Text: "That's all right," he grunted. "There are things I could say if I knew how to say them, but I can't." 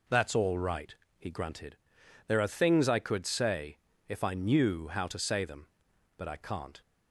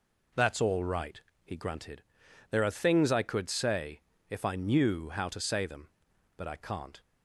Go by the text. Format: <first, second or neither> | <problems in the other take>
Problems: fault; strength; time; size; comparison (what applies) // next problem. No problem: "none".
neither | pauses between "say" and "if"; slight; the same in both